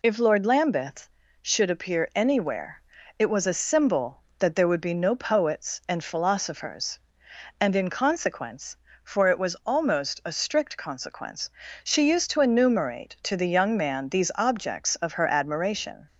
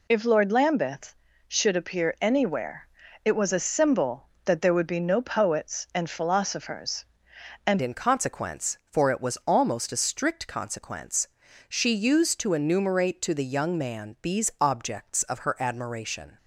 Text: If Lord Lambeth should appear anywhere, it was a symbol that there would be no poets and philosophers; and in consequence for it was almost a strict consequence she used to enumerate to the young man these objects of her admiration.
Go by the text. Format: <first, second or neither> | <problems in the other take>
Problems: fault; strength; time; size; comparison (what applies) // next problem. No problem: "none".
first | changes voice at "in"; from 7.8 s on; 8.5 s long // pauses between "consequence" and "she"; at 11.2 s; 0.42 s long; slight in the first